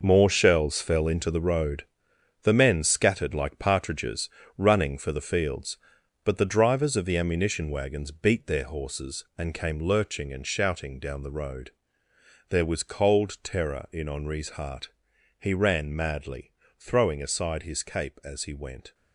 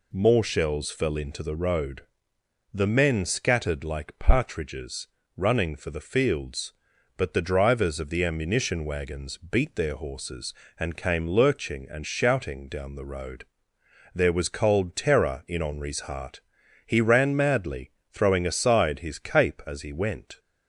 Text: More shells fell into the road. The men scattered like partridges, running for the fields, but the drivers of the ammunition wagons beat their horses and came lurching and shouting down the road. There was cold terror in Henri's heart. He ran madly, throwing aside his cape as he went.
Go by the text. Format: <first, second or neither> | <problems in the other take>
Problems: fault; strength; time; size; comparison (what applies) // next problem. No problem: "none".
second | gets quieter; strong; throughout; 10.5 dB